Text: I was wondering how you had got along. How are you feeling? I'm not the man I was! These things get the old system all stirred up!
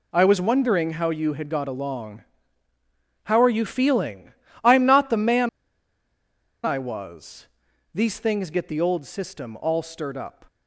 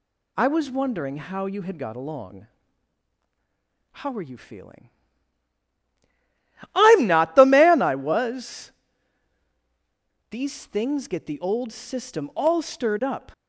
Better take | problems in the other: second | pauses between "man" and "I"; at 5.4 s; 1.1 s long

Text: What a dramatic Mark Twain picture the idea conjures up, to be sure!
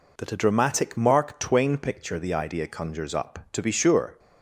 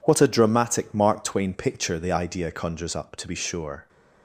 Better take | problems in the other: second | says "That" for "What"; at 0.1 s

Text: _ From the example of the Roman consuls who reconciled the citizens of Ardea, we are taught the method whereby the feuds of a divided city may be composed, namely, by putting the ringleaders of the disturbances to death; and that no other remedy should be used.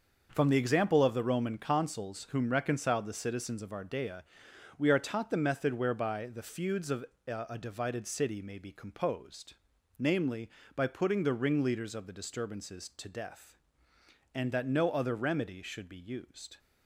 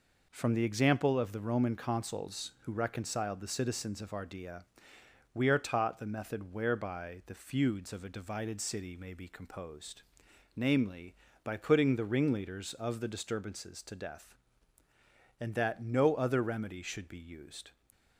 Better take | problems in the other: second | starts louder than the rest; until 1.3 s; 6 dB // says "whom" for "who"; at 2.3 s // pauses between "of" and "a"; slight; at 7.0 s; 0.22 s long

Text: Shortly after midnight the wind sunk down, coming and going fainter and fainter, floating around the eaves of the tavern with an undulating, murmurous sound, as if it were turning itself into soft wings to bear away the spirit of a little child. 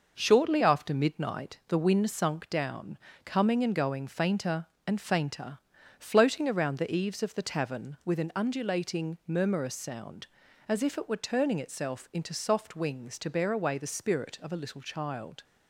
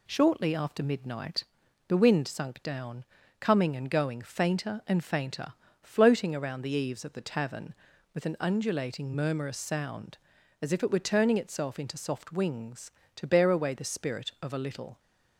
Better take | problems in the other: first | pauses between "midnight" and "the"; at 1.4 s; 0.42 s long // stops before "child"; at 14.9 s

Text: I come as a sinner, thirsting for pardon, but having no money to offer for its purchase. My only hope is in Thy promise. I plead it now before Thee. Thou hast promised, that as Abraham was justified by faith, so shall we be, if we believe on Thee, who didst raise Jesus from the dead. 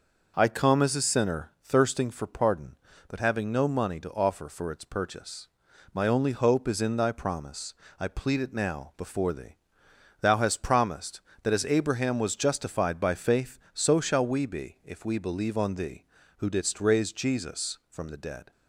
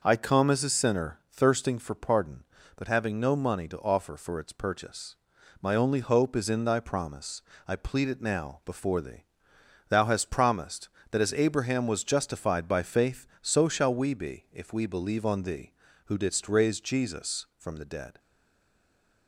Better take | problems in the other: first | stays silent after the last word; from 18.1 s on; 1.1 s long

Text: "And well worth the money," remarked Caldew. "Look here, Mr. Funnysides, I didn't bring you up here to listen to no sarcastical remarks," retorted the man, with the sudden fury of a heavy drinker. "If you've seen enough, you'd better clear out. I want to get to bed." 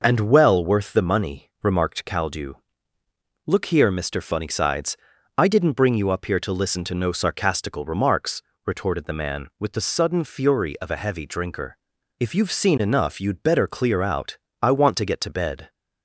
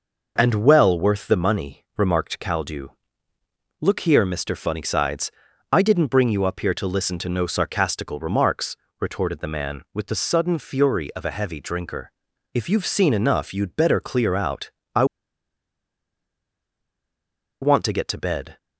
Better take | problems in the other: first | pauses between "I" and "want"; strong; at 15.0 s; 2.5 s long

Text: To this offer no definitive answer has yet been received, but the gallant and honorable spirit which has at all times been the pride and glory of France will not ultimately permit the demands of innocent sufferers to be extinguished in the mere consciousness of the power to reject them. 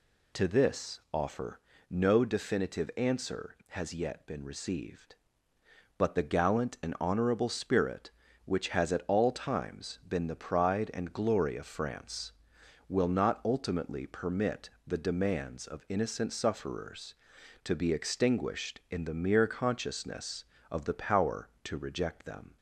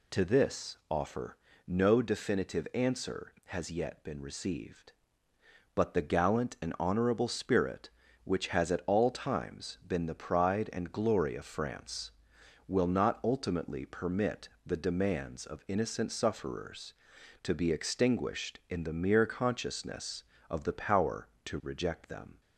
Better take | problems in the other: neither | pauses between "offer" and "no"; slight; the same in both // pauses between "permit" and "the"; slight; the same in both

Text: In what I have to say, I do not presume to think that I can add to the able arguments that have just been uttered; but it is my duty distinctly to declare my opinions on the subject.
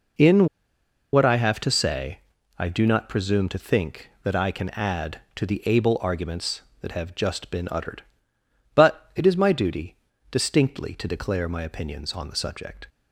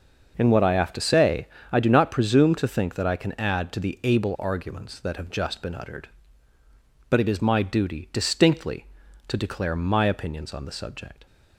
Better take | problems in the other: second | pauses between "In" and "what"; noticeable; at 0.4 s; 0.66 s long // pauses between "duty" and "distinctly"; slight; at 9.9 s; 0.36 s long

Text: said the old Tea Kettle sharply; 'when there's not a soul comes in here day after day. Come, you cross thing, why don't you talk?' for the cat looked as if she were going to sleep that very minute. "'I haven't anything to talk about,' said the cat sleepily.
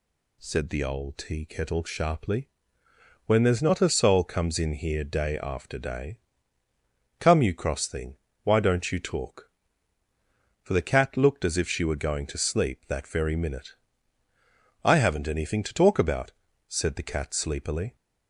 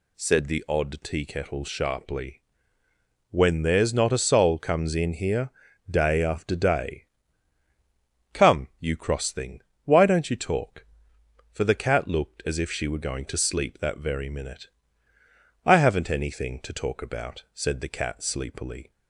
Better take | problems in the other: first | says "odd" for "old"; at 0.6 s // pauses between "here" and "day"; at 5.5 s; 0.40 s long

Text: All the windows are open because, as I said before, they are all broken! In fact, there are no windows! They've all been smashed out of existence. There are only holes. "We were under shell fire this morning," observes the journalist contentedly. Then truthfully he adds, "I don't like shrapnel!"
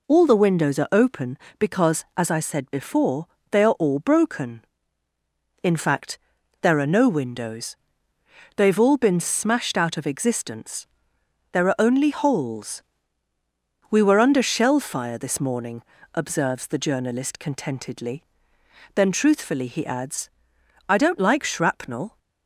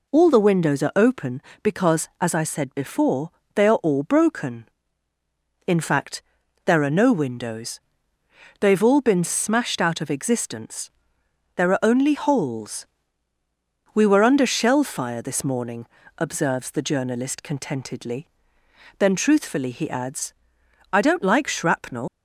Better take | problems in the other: first | leaves "shrapnel" unfinished; at 22.0 s; 140 ms

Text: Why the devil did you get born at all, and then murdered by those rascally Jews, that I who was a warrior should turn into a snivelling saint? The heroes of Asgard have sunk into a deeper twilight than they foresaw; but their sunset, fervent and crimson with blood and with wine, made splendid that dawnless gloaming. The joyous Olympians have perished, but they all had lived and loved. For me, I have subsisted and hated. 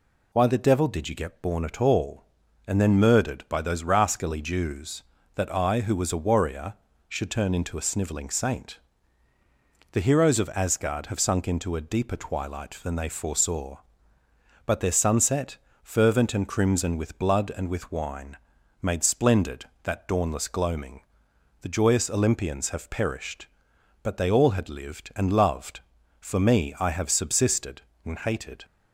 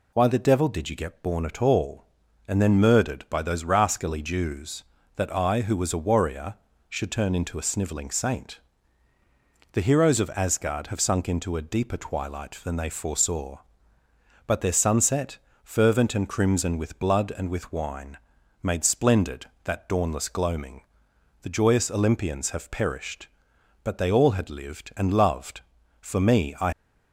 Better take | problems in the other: first | stops before "have subsisted and hated"; at 26.7 s

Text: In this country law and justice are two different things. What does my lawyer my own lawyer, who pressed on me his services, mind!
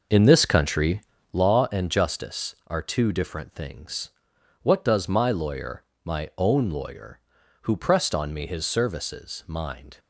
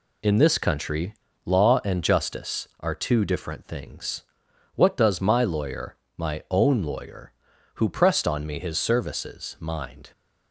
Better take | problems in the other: second | starts louder than the rest; noticeable; until 1.5 s; 5.5 dB // pauses between "country" and "law"; slight; at 1.0 s; 0.32 s long; slight in the second // pauses between "lawyer" and "my"; slight; at 5.8 s; 0.24 s long; slight in the second

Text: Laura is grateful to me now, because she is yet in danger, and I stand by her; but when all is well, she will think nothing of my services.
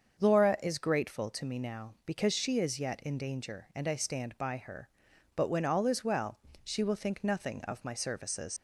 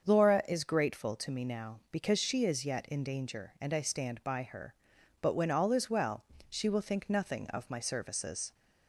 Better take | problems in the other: second | starts louder than the rest; until 1.2 s; 7 dB; also in the second // leaves "services" unfinished; at 8.5 s; 115 ms

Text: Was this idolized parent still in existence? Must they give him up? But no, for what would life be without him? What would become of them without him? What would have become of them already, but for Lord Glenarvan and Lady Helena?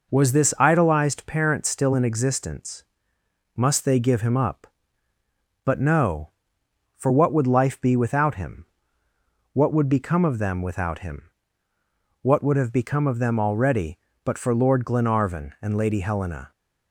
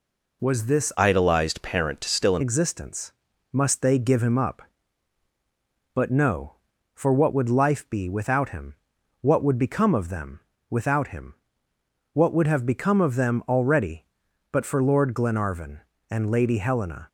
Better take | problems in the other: first | changes voice from "idolized" to "in"; from 0.9 to 2.4 s; 1.5 s long // pauses between "them" and "without"; slight; at 10.3 s; 0.30 s long

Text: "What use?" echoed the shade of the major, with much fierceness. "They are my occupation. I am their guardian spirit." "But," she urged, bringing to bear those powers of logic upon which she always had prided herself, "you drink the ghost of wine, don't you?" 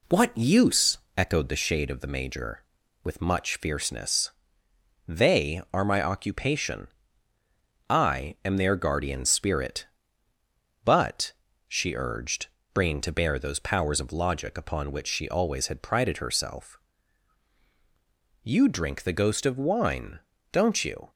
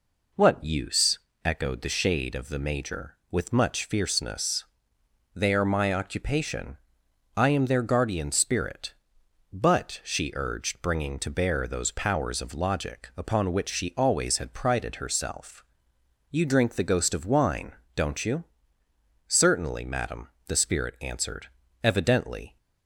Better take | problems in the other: first | goes on to say "Certainly madam the spirit answered evidently"; strong; from 19.2 s on; 3.3 s long

